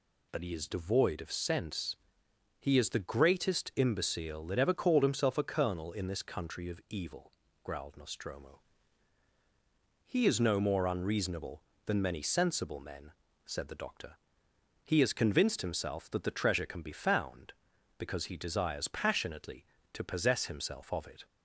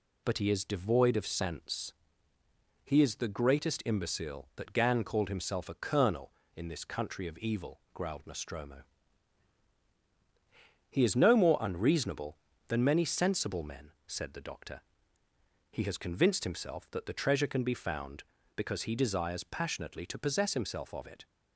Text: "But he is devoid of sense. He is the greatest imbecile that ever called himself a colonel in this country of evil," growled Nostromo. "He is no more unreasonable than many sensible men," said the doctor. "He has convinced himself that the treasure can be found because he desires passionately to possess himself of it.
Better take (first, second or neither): first